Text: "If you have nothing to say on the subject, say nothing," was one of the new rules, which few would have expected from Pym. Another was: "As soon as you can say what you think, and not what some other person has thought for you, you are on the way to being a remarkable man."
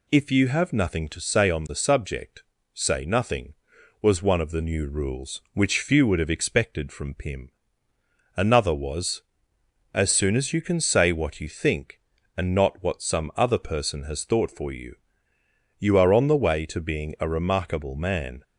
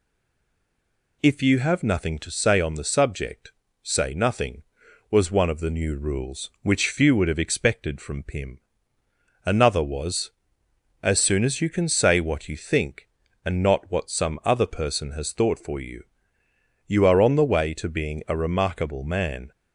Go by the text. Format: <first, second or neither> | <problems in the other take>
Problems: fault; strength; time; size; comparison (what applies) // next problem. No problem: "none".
first | stays silent before the first word; noticeable; until 1.2 s; 1.2 s long